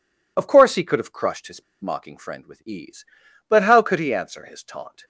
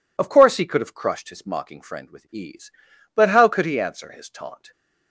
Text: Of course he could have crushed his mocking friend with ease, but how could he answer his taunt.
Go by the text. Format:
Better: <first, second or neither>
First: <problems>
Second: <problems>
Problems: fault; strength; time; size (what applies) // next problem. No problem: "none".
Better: second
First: pauses between "his" and "mocking"; slight; at 1.6 s; 0.17 s long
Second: none